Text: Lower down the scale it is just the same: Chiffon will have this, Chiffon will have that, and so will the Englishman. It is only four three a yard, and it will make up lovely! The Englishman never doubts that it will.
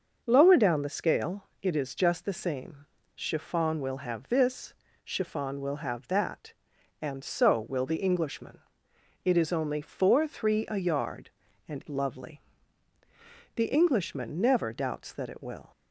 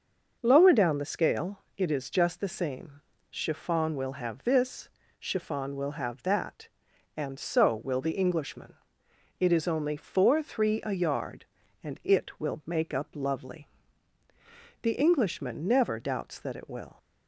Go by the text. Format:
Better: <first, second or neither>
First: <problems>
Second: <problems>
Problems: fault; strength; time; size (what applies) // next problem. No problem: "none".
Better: second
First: pauses between "scale" and "it"; slight; at 1.4 s; 0.16 s long // skips "it will make up"; at 11.8 s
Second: pauses between "scale" and "it"; slight; at 1.6 s; 0.16 s long